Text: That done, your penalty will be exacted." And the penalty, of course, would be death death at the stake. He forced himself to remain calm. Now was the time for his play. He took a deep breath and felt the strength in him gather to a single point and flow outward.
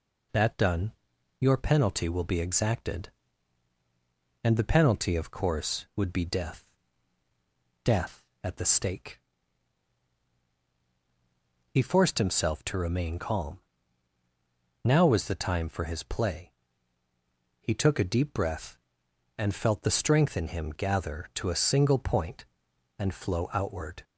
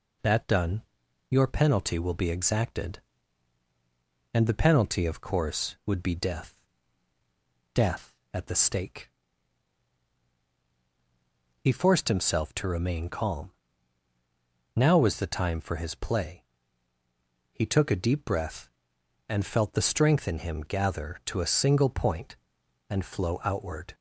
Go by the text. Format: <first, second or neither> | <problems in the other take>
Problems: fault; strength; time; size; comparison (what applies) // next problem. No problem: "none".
neither | pauses between "death" and "death"; the same in both